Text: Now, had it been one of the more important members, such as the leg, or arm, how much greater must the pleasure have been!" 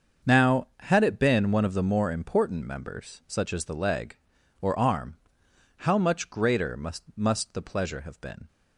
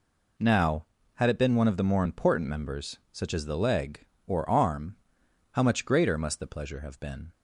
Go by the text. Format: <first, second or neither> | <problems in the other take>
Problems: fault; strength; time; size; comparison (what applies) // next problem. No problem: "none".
second | starts louder than the rest; until 1.3 s; 6.5 dB // says "must" twice; at 7.1 s